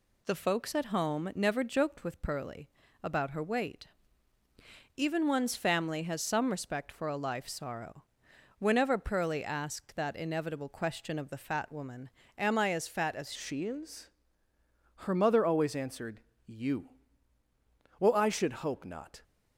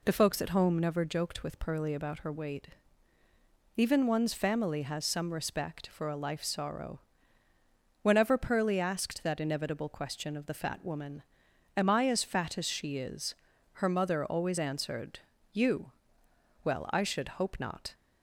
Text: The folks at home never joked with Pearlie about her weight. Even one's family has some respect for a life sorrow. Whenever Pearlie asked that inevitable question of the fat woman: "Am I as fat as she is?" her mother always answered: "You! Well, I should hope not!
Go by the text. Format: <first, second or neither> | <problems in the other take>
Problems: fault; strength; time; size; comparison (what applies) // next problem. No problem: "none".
second | pauses between "Pearlie" and "about"; slight; at 2.6 s; 0.34 s long // changes voice at "she"; from 13.3 s on; 5.9 s long